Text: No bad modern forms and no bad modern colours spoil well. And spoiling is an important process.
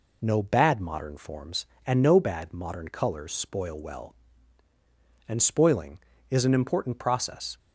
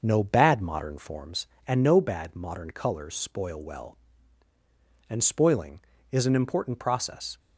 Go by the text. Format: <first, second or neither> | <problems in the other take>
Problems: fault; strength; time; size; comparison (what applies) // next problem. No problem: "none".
first | starts louder than the rest; noticeable; until 1.3 s; 6 dB